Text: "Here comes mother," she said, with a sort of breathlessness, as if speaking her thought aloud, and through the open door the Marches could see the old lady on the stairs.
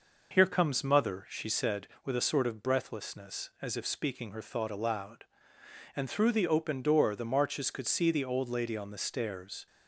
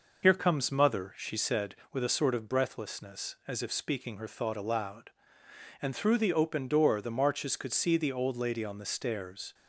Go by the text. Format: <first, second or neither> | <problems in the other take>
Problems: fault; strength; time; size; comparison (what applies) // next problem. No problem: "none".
first | loses the start of "Here"; at 0.2 s; 45 ms